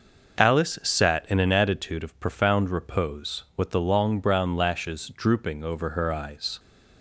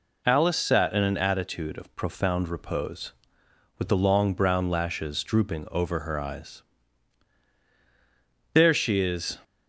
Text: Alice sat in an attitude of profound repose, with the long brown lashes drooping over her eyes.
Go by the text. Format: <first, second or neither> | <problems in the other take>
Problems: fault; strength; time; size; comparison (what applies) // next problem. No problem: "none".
first | goes on to say "There she is"; noticeable; from 8.5 s on; 0.86 s long